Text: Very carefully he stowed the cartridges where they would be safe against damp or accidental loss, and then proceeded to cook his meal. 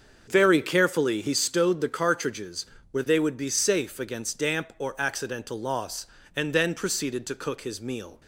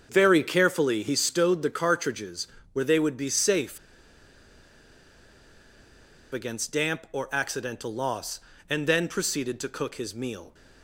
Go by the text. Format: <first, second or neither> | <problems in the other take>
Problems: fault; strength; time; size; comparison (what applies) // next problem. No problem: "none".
first | starts louder than the rest; until 1.1 s; 6.5 dB; also in the first // pauses between "cartridges" and "where"; slight; at 2.4 s; 0.24 s long; slight in the first // pauses between "safe" and "against"; strong; at 3.7 s; 2.5 s long